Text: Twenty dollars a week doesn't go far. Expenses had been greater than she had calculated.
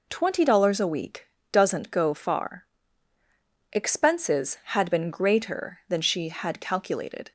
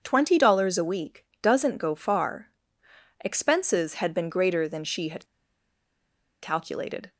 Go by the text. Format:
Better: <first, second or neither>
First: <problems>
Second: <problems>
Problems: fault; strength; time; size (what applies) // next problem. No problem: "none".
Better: first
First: pauses between "week" and "doesn't"; slight; at 1.2 s; 0.26 s long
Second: starts louder than the rest; until 1.0 s; 7 dB // pauses between "week" and "doesn't"; slight; at 1.2 s; 0.18 s long // pauses between "had" and "calculated"; at 5.2 s; 1.1 s long